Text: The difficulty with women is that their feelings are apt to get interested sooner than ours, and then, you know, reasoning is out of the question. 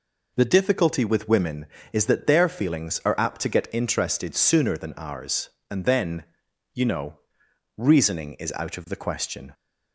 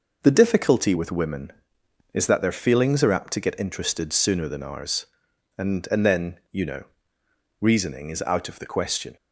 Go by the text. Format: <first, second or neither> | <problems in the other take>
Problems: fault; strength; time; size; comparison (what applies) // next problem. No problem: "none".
first | says "and" twice; at 5.9 s